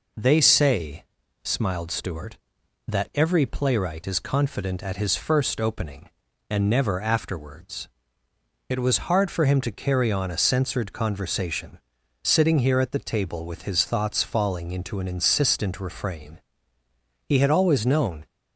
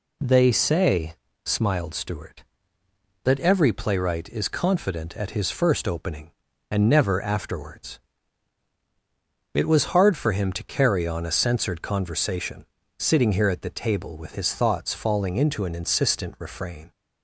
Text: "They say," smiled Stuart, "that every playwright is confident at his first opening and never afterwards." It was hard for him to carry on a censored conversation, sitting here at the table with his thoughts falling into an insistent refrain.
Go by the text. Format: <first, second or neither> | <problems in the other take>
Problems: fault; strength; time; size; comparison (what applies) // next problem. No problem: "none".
second | goes on to say "He had always known"; noticeable; from 17.2 s on; 0.98 s long